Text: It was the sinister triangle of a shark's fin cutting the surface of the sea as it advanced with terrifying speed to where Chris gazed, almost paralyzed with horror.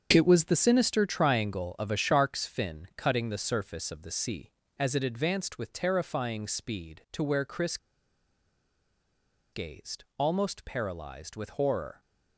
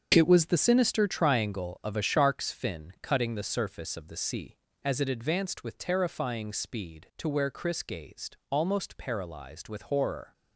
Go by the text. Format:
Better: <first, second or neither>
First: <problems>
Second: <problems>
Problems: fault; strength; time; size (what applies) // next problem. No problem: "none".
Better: second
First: starts louder than the rest; until 1.1 s; 6.5 dB // pauses between "Chris" and "gazed"; strong; at 7.7 s; 1.7 s long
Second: starts louder than the rest; until 1.1 s; 6.5 dB